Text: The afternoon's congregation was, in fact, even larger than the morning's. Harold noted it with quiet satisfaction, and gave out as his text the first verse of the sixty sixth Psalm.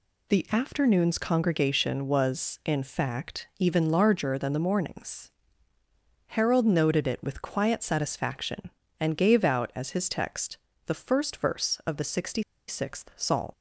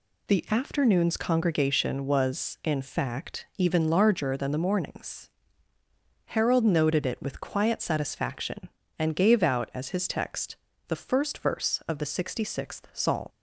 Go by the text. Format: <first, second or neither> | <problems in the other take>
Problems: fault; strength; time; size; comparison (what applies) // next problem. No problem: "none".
second | pauses between "text" and "the"; slight; at 10.5 s; 0.30 s long; slight in the second // pauses between "sixty" and "sixth"; slight; at 12.4 s; 0.25 s long